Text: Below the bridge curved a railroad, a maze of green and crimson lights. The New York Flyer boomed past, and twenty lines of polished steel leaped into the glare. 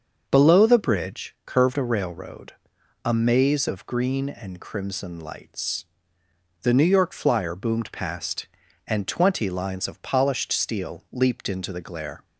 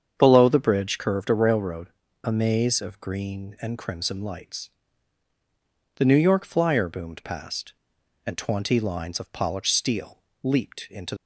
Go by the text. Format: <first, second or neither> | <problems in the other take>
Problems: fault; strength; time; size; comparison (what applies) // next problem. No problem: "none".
first | starts louder than the rest; strong; until 1.1 s; 7.5 dB; also in the first // pauses between "steel" and "leaped"; slight; at 10.2 s; 0.20 s long // stops before "the glare"; at 11.1 s